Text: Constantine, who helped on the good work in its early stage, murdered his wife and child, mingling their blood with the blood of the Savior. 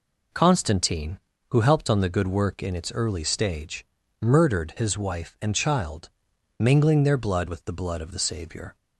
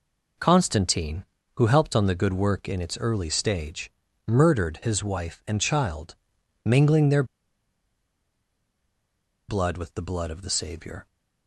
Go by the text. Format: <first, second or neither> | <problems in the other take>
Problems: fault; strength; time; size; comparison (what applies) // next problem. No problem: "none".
first | pauses between "their" and "blood"; strong; at 7.2 s; 2.2 s long